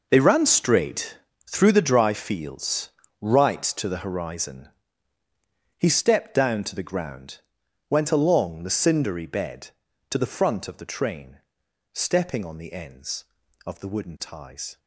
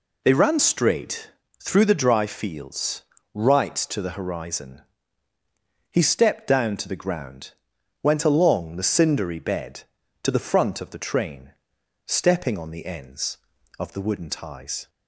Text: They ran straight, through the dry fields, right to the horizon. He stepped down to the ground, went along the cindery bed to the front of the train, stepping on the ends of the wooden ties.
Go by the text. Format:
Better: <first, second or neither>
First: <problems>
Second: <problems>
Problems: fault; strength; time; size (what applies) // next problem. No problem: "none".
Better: second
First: gets quieter; strong; throughout; 13.5 dB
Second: none